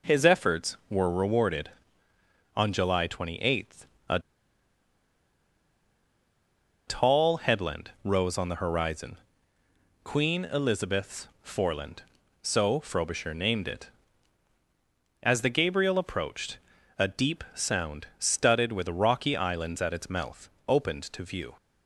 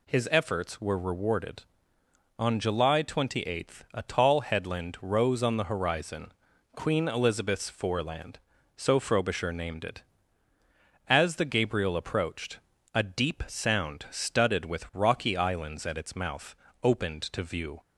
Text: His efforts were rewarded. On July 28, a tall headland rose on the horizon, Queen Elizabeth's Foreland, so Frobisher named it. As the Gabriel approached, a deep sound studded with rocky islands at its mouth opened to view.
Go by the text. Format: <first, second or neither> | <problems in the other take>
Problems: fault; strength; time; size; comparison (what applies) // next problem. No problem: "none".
second | pauses between "a" and "tall"; strong; at 4.1 s; 2.6 s long // pauses between "Elizabeth's" and "Foreland"; slight; at 11.2 s; 0.18 s long // pauses between "mouth" and "opened"; slight; at 20.4 s; 0.20 s long; slight in the second